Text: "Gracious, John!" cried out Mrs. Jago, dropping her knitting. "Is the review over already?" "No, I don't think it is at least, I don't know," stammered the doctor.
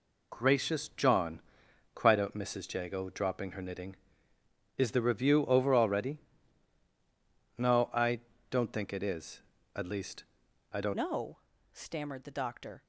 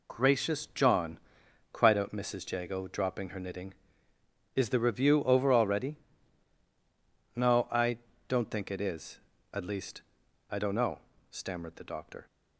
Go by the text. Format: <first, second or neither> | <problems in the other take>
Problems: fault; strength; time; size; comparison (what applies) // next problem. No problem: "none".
second | pauses between "I" and "don't"; slight; at 8.1 s; 0.30 s long; slight in the second // changes voice at "know"; from 10.9 s on; 1.9 s long